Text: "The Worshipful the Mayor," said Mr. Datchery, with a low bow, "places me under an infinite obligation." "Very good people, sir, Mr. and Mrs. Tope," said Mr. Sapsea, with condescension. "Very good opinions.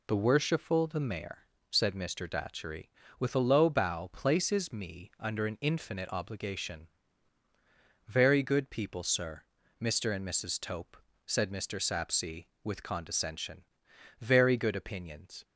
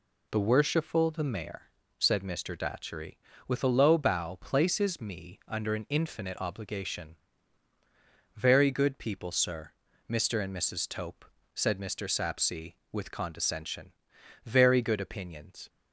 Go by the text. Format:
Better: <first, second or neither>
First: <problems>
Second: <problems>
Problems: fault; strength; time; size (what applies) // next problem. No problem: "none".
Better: neither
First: none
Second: none